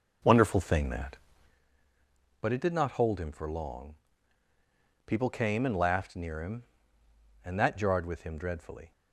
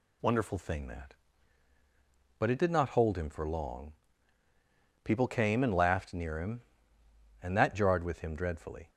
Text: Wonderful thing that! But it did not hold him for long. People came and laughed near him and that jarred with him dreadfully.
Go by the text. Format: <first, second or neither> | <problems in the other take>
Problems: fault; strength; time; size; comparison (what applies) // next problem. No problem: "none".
second | starts louder than the rest; noticeable; until 1.6 s; 5 dB